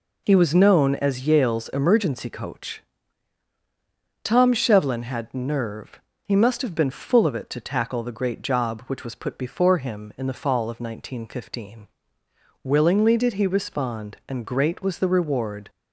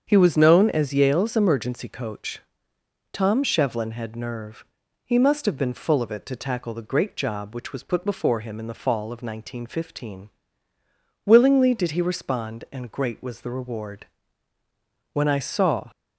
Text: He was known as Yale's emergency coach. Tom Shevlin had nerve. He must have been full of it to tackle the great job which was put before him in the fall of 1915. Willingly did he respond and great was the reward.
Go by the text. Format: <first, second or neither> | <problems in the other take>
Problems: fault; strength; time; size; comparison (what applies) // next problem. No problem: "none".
first | starts louder than the rest; strong; until 1.0 s; 7.5 dB // goes on to say "When I saw"; noticeable; from 15.1 s on; 0.78 s long